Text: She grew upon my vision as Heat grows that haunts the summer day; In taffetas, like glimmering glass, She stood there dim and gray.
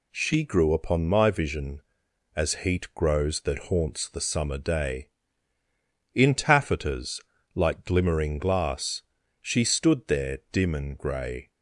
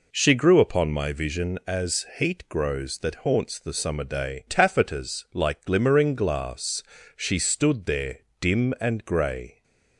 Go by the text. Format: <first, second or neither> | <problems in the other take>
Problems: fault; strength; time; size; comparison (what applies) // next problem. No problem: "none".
first | skips "In"; at 4.4 s // pauses between "there" and "dim"; slight; at 8.1 s; 0.20 s long